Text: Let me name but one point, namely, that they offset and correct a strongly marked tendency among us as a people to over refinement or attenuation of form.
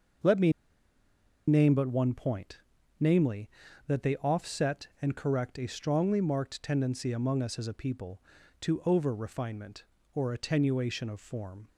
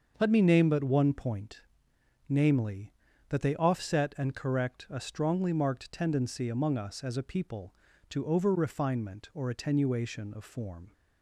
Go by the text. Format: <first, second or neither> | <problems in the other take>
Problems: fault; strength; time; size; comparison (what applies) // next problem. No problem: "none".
second | starts louder than the rest; until 2.2 s; 6 dB; also in the second // pauses between "me" and "name"; noticeable; at 0.5 s; 0.95 s long